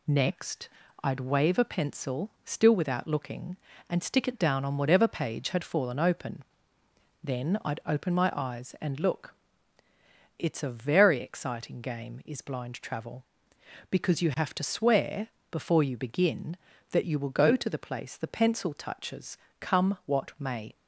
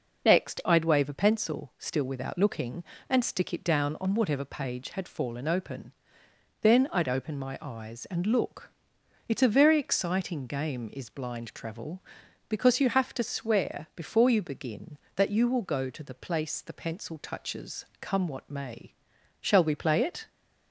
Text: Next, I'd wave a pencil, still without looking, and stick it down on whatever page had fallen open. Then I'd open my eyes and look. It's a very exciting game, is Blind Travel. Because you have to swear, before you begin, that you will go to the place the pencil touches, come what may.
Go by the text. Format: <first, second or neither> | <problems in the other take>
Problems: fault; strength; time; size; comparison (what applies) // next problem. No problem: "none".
first | goes on to say "Shall we play it"; noticeable; from 19.4 s on; 0.88 s long